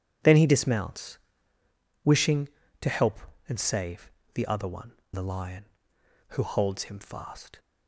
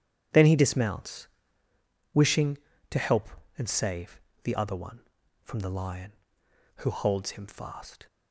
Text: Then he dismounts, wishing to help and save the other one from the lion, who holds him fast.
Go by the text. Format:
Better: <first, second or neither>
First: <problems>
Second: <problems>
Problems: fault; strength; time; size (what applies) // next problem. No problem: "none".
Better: second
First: pauses between "save" and "the"; slight; at 4.1 s; 0.24 s long // skips "from"; at 5.0 s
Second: pauses between "save" and "the"; slight; at 4.1 s; 0.24 s long